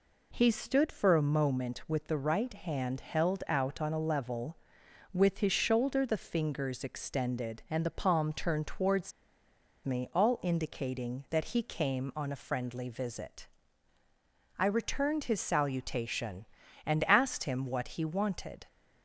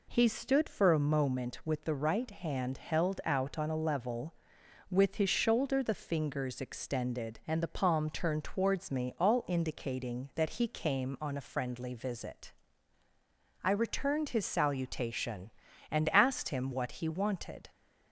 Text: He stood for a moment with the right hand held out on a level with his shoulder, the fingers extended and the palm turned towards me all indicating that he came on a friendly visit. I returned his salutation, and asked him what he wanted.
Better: second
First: pauses between "towards" and "me"; noticeable; at 9.1 s; 0.72 s long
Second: none

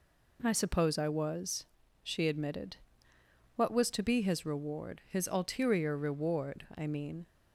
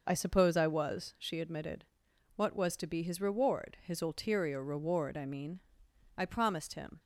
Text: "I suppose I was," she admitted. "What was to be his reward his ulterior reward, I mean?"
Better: first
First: none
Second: goes on to say "I promised him"; noticeable; from 6.1 s on; 0.84 s long

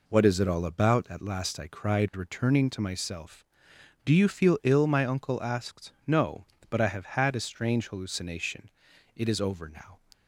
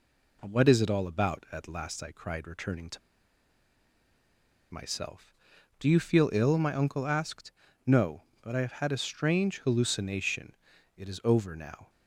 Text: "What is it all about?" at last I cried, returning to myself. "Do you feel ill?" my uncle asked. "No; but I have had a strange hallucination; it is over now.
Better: first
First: none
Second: pauses between "to" and "myself"; strong; at 3.0 s; 1.7 s long

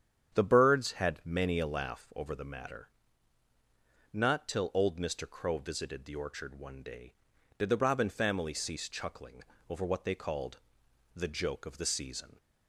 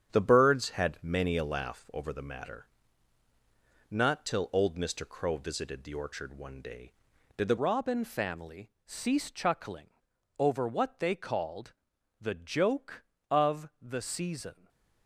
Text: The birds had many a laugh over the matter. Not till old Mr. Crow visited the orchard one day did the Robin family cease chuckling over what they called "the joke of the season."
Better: first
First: starts louder than the rest; strong; until 1.3 s; 8.5 dB // pauses between "chuckling" and "over"; slight; at 9.4 s; 0.26 s long // pauses between "called" and "the"; noticeable; at 10.6 s; 0.54 s long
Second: starts louder than the rest; strong; until 1.1 s; 8.5 dB // changes voice at "Robin"; from 7.5 s on; 7.1 s long // pauses between "chuckling" and "over"; noticeable; at 9.9 s; 0.48 s long // pauses between "called" and "the"; noticeable; at 11.7 s; 0.48 s long // stays silent after the last word; slight; from 14.5 s on; 0.5 s long

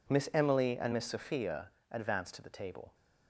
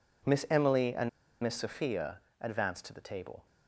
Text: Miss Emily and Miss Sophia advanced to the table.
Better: first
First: pauses between "Sophia" and "advanced"; slight; at 1.6 s; 0.20 s long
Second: pauses between "and" and "Miss"; slight; at 1.0 s; 0.33 s long // pauses between "Sophia" and "advanced"; slight; at 2.1 s; 0.20 s long

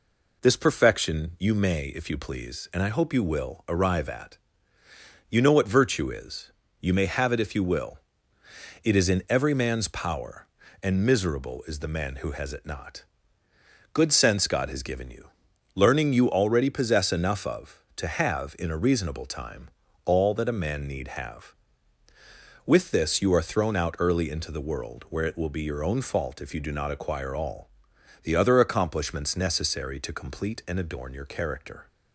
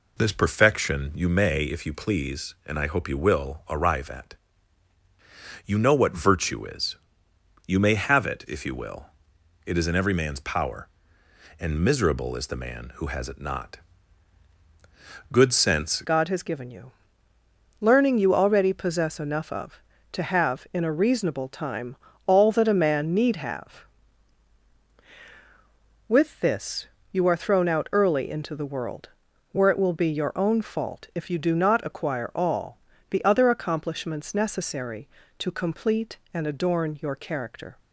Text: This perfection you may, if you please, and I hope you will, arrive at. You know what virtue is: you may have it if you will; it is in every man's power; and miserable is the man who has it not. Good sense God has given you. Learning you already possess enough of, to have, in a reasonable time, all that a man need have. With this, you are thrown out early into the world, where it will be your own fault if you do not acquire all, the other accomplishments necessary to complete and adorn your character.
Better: first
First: none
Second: changes voice at "God"; from 16.0 s on; 21.7 s long

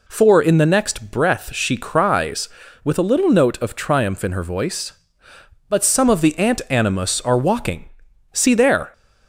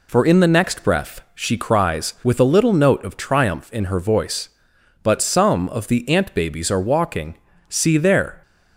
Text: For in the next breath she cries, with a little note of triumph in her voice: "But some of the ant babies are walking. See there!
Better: second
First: says "animus" for "babies"; at 6.6 s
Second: none

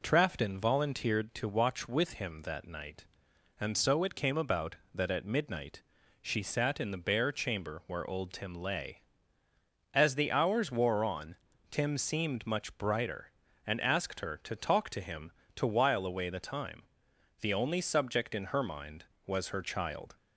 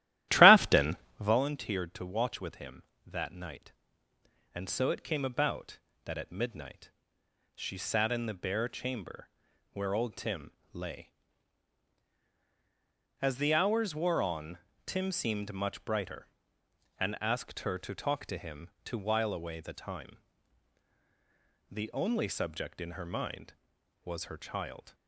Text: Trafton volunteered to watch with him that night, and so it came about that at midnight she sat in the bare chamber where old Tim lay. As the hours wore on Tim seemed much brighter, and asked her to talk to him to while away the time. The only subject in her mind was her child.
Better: first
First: pauses between "midnight" and "she"; at 5.8 s; 0.38 s long // pauses between "on" and "Tim"; slight; at 11.3 s; 0.34 s long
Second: starts louder than the rest; strong; until 1.4 s; 14 dB // pauses between "Trafton" and "volunteered"; slight; at 0.9 s; 0.24 s long // pauses between "midnight" and "she"; noticeable; at 6.9 s; 0.64 s long // pauses between "chamber" and "where"; at 9.2 s; 0.44 s long // pauses between "Tim" and "lay"; slight; at 10.5 s; 0.22 s long // pauses between "on" and "Tim"; slight; at 14.5 s; 0.26 s long

